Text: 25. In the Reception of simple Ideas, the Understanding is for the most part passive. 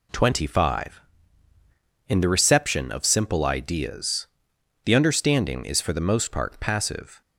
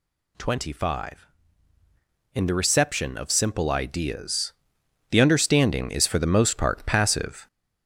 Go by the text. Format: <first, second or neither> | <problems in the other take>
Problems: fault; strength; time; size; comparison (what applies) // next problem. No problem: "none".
first | gets louder; noticeable; throughout; 4 dB